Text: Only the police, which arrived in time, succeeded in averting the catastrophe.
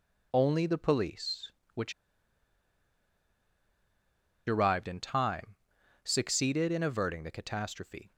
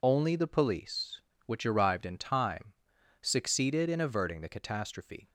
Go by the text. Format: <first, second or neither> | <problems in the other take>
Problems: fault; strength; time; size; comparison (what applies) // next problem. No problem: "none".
second | pauses between "which" and "arrived"; strong; at 1.9 s; 2.5 s long